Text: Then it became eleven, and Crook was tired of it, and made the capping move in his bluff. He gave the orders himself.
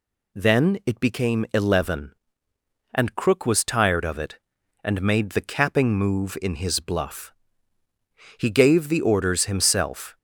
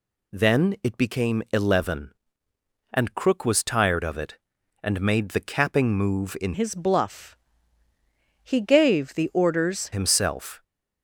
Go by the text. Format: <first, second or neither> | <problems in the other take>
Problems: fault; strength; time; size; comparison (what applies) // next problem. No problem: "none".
first | changes voice from "his" to "orders"; from 6.5 to 9.9 s; 3.4 s long